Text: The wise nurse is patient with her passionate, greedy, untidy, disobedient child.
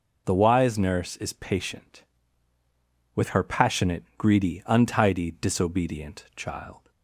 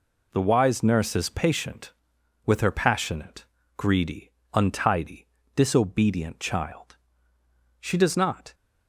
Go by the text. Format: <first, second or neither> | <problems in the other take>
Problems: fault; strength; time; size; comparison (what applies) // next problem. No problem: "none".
first | goes on to say "She does not"; noticeable; from 7.7 s on; 0.74 s long